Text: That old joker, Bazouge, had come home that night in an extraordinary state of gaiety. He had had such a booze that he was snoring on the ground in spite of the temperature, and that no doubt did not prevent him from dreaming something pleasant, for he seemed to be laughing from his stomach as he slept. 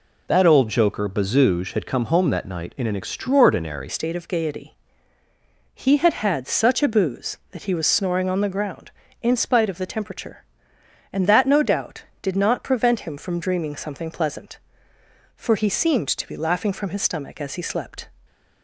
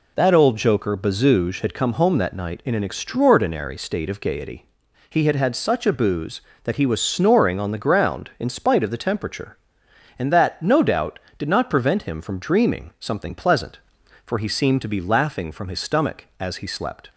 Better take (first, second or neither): second